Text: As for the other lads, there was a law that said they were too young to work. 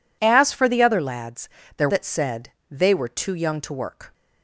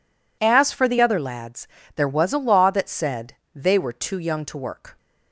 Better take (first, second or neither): second